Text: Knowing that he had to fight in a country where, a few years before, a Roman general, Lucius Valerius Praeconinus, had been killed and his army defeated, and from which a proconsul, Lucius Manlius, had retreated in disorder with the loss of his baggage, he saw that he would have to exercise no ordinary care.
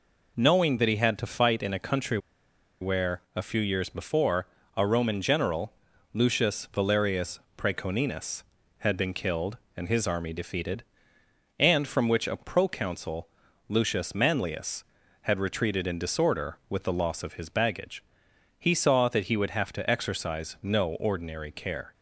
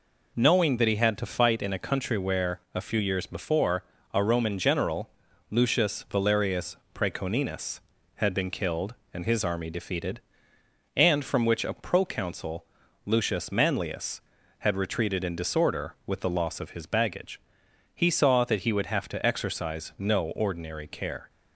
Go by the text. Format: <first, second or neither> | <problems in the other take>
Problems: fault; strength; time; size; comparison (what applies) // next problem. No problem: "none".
second | pauses between "country" and "where"; noticeable; at 2.1 s; 0.62 s long // pauses between "Valerius" and "Praeconinus"; slight; at 7.3 s; 0.18 s long; slight in the second